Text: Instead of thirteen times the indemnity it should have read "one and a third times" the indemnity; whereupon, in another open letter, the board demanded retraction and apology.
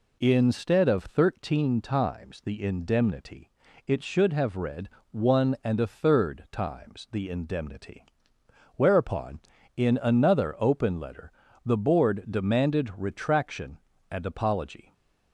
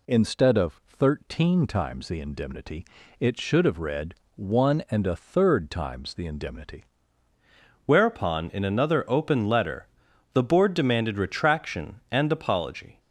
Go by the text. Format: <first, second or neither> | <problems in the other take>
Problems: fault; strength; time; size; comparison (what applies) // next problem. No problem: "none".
first | pauses between "indemnity" and "it"; slight; at 2.8 s; 0.36 s long; also in the first // pauses between "read" and "one"; slight; at 4.1 s; 0.22 s long; slight in the first // changes voice at "whereupon"; from 7.8 s on; 5.1 s long